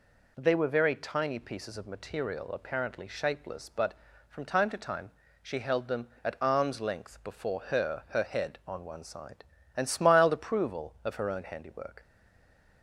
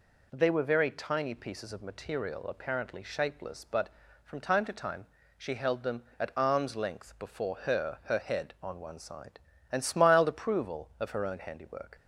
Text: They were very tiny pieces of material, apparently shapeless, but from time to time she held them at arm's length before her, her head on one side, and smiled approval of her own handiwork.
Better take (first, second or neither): second